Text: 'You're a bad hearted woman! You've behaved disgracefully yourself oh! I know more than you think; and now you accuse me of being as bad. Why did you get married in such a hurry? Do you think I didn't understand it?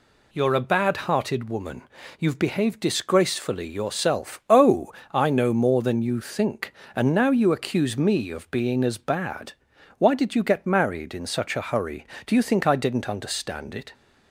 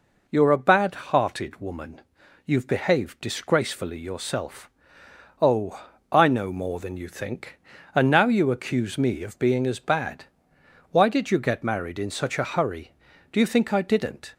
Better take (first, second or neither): first